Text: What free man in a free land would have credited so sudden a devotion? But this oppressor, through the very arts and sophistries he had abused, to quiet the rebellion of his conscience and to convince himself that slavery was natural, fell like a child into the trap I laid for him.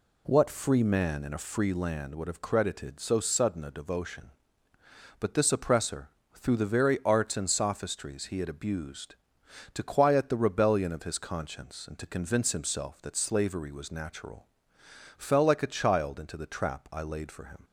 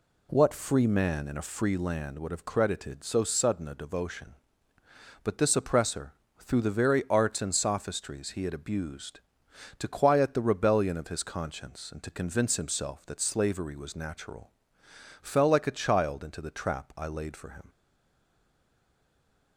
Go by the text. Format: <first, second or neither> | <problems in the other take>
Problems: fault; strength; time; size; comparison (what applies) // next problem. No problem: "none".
first | stays silent after the last word; noticeable; from 17.6 s on; 1.9 s long